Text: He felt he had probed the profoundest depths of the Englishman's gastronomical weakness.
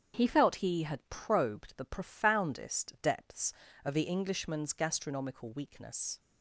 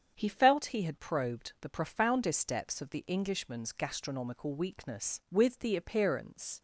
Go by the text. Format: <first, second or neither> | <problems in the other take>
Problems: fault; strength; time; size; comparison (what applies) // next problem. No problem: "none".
first | starts louder than the rest; strong; until 1.1 s; 7.5 dB; strong in the first // goes on to say "With the appearance"; noticeable; from 5.2 s on; 1.3 s long